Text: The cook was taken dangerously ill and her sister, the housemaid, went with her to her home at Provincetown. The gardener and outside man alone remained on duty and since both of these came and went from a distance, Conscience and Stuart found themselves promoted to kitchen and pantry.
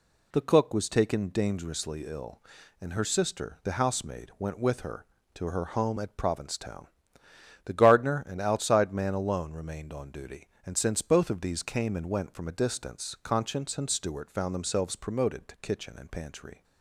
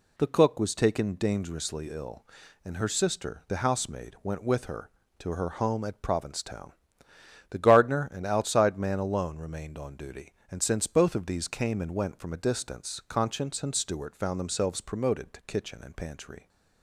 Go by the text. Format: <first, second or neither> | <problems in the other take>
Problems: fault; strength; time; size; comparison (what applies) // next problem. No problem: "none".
neither | none